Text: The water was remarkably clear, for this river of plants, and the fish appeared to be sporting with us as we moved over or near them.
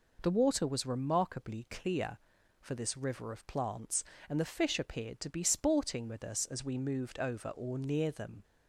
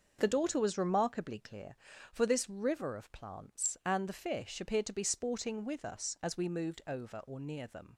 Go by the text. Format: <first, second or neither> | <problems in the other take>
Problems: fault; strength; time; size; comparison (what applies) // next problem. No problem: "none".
first | starts louder than the rest; until 1.2 s; 6.5 dB // says "daughter" for "water"; at 0.2 s